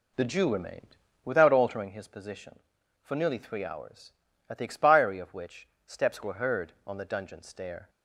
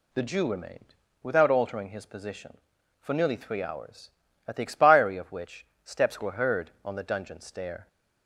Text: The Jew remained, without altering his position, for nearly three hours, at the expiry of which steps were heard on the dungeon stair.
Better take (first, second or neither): second